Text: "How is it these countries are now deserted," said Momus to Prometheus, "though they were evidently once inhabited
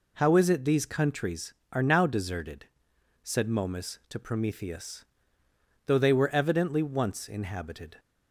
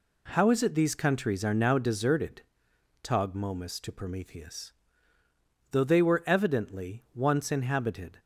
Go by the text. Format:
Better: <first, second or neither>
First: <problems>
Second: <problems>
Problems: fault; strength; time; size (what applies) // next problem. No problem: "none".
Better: first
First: none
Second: says "tog" for "said"; at 3.0 s